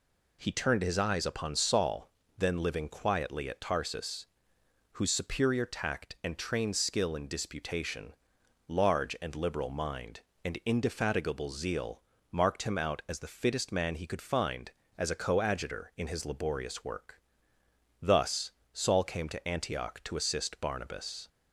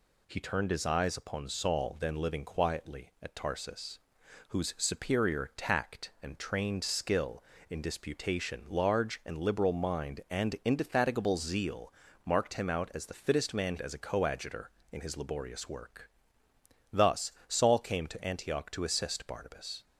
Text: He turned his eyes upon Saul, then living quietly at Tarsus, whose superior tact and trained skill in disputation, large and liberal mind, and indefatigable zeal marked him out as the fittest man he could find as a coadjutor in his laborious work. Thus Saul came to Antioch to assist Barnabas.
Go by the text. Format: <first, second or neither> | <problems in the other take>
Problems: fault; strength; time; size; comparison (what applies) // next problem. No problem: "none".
first | pauses between "zeal" and "marked"; slight; at 11.9 s; 0.32 s long; slight in the first // skips "he could find"; at 13.7 s // pauses between "Thus" and "Saul"; slight; at 17.3 s; 0.16 s long; slight in the first